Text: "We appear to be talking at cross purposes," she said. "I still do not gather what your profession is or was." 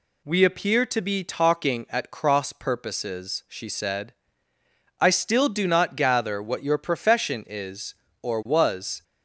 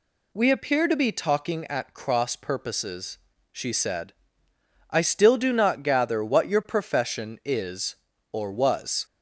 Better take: neither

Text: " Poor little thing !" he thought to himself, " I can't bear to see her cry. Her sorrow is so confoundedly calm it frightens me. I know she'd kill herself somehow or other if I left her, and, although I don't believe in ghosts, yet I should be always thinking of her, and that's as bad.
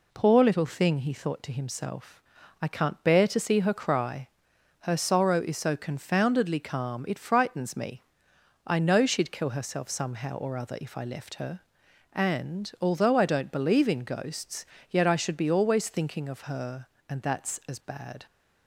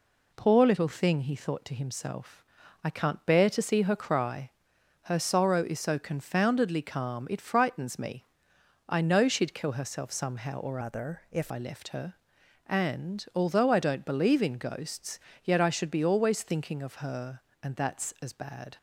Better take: first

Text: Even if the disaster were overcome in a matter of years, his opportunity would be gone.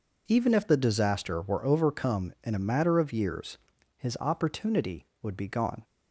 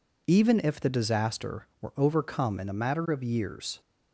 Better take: first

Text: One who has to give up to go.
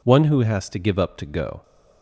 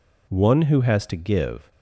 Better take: first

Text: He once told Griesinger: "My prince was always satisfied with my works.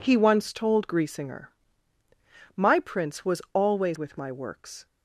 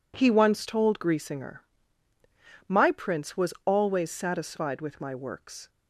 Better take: second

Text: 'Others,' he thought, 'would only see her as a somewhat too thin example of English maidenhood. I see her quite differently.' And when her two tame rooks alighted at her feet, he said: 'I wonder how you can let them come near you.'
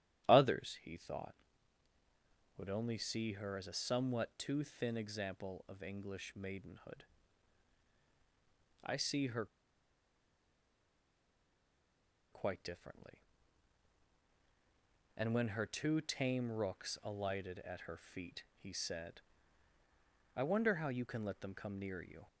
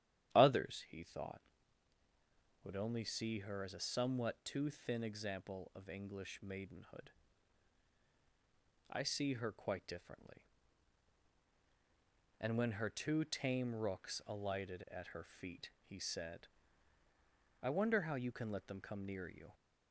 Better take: second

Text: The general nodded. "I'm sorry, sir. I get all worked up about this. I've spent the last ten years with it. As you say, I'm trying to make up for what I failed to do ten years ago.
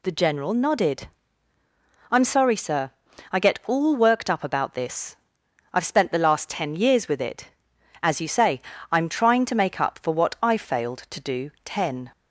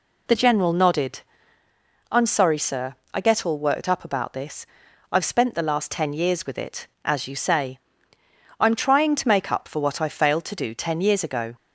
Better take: second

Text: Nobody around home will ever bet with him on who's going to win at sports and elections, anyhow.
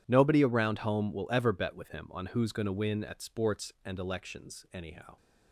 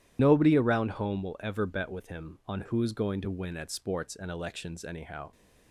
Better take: first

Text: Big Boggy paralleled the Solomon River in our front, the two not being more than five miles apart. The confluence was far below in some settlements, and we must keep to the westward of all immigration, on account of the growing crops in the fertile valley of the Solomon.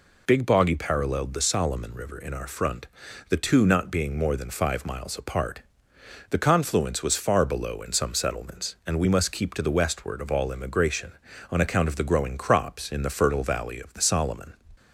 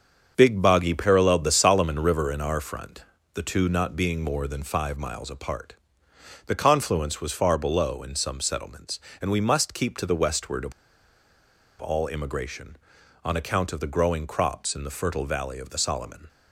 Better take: first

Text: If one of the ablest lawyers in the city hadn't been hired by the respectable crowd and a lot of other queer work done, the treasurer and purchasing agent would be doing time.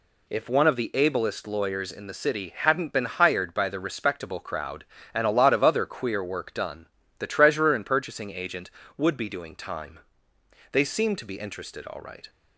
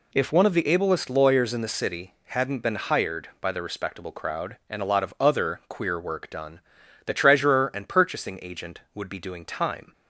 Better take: second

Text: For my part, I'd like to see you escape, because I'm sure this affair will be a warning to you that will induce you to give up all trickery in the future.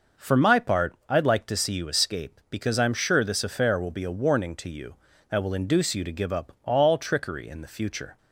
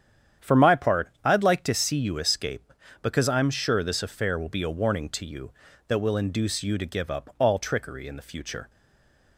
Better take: first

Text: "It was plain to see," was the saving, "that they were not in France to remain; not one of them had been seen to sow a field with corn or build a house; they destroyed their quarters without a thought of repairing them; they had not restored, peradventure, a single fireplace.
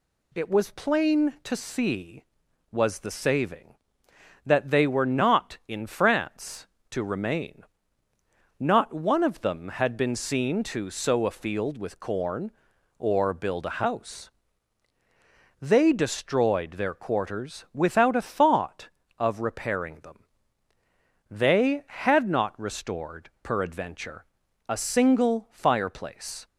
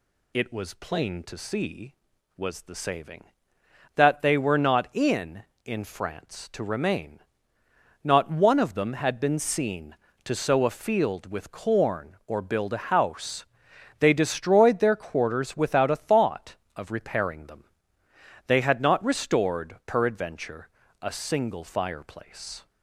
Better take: first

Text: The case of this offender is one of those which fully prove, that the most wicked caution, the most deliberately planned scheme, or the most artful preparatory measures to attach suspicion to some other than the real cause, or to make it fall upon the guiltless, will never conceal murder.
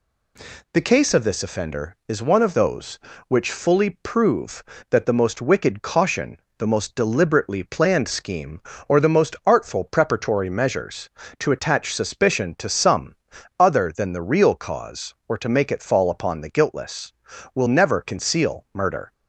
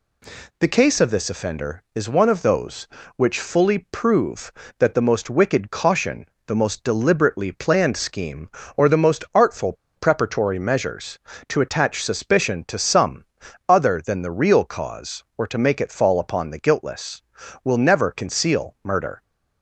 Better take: first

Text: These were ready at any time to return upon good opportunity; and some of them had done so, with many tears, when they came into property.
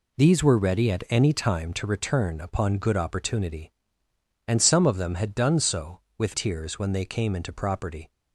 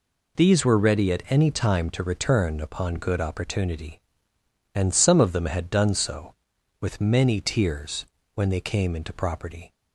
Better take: second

